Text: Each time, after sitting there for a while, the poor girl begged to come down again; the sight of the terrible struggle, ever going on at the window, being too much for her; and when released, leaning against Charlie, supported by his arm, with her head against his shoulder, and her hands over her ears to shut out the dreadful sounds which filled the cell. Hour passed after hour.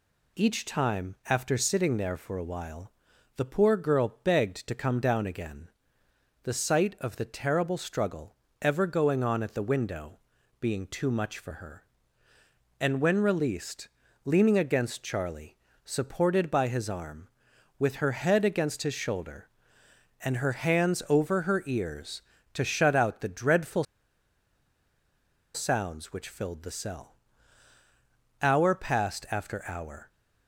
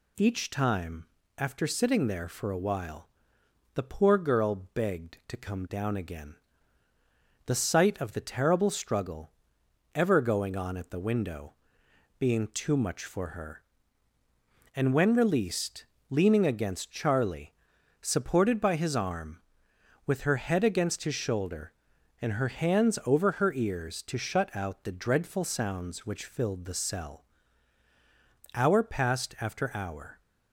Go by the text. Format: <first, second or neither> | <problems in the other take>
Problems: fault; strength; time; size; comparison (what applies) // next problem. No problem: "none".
second | pauses between "dreadful" and "sounds"; strong; at 23.8 s; 1.7 s long